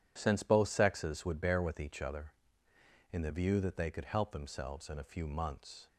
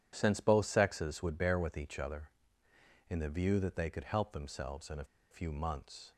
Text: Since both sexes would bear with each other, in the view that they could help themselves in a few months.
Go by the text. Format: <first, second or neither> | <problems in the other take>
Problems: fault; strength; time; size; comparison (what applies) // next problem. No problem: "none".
first | pauses between "a" and "few"; slight; at 5.0 s; 0.27 s long